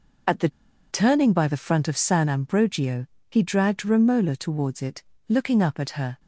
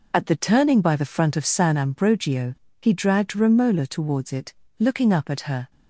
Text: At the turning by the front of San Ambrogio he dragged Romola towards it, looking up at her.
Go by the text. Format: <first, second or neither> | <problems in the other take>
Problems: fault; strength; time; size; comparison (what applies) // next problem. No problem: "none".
second | pauses between "the" and "turning"; at 0.4 s; 0.41 s long // pauses between "Ambrogio" and "he"; slight; at 3.0 s; 0.26 s long; slight in the second